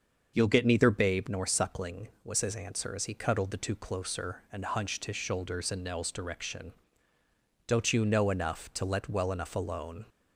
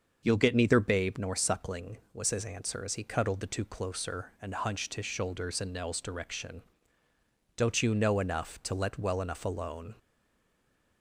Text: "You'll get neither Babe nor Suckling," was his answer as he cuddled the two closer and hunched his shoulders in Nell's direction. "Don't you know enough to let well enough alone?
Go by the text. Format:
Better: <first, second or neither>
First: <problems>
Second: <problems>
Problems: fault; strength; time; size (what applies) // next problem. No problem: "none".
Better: first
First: starts louder than the rest; until 1.3 s; 6.5 dB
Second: starts louder than the rest; until 1.2 s; 6.5 dB // stays silent after the last word; from 9.9 s on; 1.1 s long